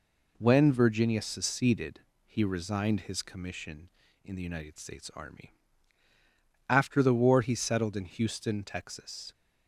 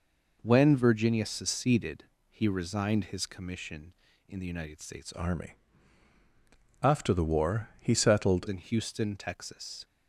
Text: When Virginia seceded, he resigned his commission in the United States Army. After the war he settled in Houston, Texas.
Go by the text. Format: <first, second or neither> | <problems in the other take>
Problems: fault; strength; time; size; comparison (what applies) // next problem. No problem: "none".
first | changes voice from "Army" to "settled"; from 5.1 to 8.4 s; 3.3 s long